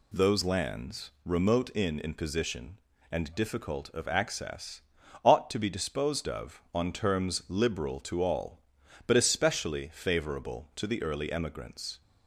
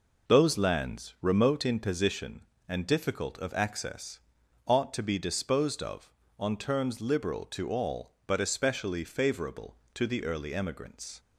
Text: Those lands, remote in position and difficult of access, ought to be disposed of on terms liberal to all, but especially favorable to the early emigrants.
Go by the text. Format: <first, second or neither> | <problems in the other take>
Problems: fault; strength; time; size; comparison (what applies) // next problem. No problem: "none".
second | says "in" twice; at 1.9 s